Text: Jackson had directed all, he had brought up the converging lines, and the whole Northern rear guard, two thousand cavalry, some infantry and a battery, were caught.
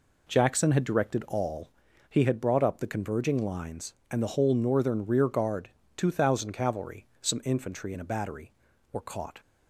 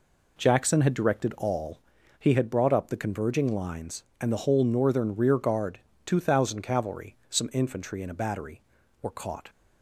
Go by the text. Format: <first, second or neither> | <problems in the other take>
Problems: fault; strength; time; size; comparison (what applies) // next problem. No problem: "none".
neither | none